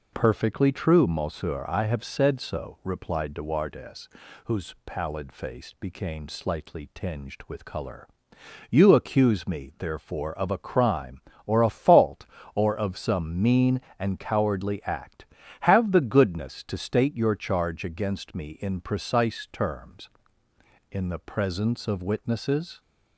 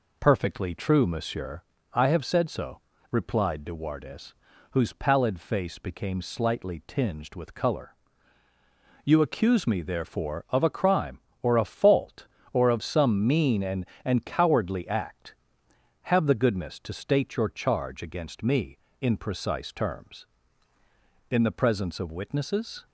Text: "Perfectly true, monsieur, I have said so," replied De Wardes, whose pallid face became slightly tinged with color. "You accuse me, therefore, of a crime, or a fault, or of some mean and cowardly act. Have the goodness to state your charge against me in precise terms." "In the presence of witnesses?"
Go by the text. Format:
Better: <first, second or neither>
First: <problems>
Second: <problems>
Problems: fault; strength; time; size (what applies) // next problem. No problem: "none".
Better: first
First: none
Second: says "and" twice; at 14.0 s